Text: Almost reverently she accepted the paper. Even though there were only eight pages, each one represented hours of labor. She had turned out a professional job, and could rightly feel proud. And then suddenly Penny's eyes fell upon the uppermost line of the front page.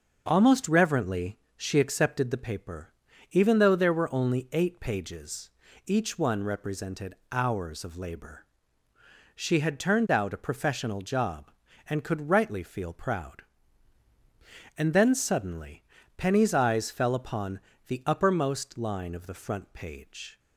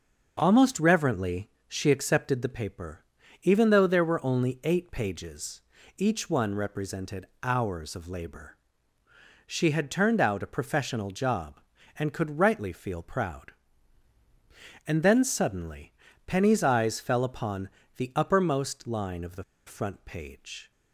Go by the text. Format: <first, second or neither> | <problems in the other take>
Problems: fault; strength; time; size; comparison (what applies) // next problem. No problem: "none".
first | pauses between "reverently" and "she"; slight; at 1.5 s; 0.16 s long; slight in the first // pauses between "represented" and "hours"; slight; at 7.2 s; 0.16 s long; slight in the first // pauses between "suddenly" and "Penny's"; slight; at 15.9 s; 0.36 s long; slight in the first // pauses between "upon" and "the"; slight; at 17.6 s; 0.28 s long; slight in the first // pauses between "the" and "front"; slight; at 19.4 s; 0.24 s long